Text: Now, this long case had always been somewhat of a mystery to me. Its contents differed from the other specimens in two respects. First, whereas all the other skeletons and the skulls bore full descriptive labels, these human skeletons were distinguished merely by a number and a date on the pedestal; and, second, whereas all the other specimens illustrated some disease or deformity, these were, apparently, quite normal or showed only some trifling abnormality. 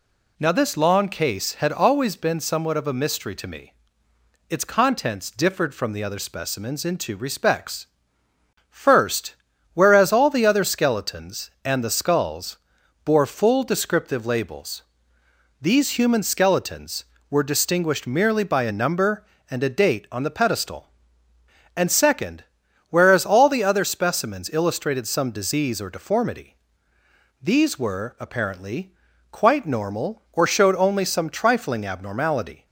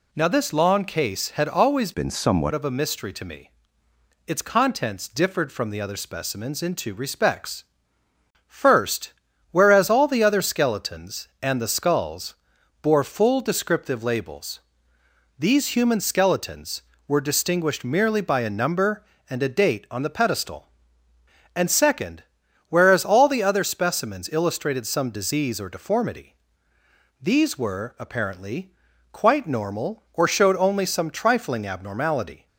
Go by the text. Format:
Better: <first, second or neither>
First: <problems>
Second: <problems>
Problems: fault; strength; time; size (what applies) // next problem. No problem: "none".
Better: first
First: pauses between "skulls" and "bore"; noticeable; at 12.5 s; 0.48 s long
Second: changes voice from "been" to "somewhat"; from 1.9 to 2.5 s; 0.6 s long // pauses between "skulls" and "bore"; noticeable; at 12.3 s; 0.48 s long